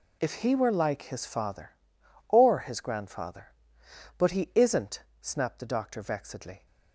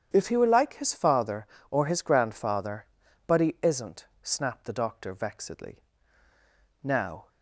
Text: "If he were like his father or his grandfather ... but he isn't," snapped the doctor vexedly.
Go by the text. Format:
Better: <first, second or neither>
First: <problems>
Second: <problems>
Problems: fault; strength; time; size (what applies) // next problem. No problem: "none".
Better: first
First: none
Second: starts louder than the rest; strong; until 1.1 s; 9 dB // goes on to say "Now"; slight; from 6.8 s on; 0.44 s long